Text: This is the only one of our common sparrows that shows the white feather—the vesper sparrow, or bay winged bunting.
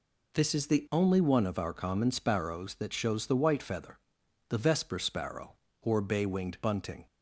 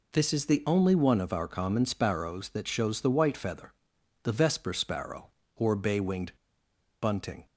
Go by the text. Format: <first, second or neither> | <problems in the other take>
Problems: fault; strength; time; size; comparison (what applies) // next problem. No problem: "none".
first | pauses between "winged" and "bunting"; noticeable; at 6.3 s; 0.67 s long